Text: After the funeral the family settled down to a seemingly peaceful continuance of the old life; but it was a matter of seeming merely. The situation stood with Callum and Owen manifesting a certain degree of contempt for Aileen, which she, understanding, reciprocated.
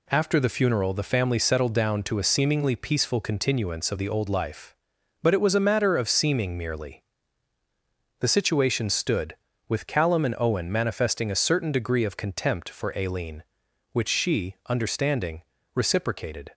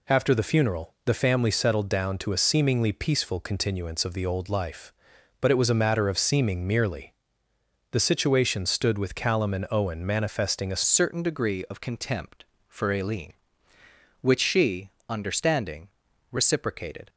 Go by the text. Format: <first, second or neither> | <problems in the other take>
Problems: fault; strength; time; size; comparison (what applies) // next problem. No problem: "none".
first | changes voice at "certain"; from 10.8 s on; 6.2 s long